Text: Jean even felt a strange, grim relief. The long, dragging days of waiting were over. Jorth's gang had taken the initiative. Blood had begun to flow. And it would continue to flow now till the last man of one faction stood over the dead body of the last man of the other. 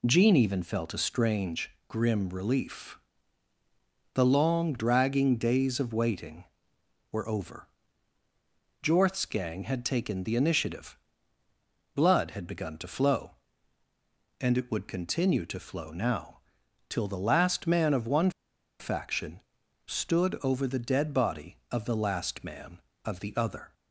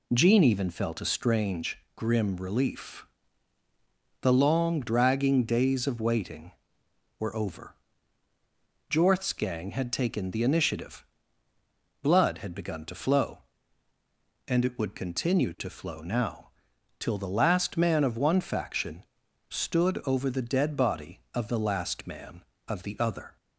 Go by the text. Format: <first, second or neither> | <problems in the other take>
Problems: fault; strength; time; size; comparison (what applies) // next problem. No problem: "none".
second | pauses between "now" and "till"; noticeable; at 16.3 s; 0.48 s long; noticeable in the second // pauses between "one" and "faction"; noticeable; at 18.2 s; 0.49 s long // pauses between "faction" and "stood"; noticeable; at 19.3 s; 0.48 s long; noticeable in the second